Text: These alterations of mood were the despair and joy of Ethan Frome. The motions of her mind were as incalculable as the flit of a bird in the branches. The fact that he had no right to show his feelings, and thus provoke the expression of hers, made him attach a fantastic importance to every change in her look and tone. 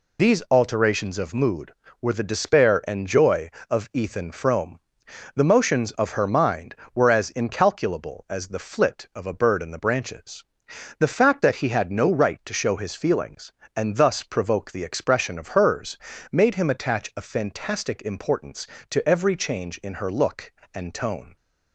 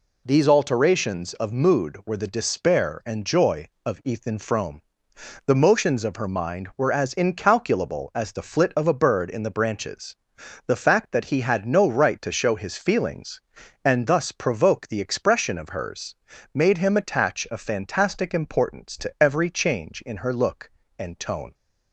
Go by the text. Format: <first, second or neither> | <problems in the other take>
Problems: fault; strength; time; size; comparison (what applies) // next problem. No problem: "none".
second | loses the start of "These"; at 0.1 s; 55 ms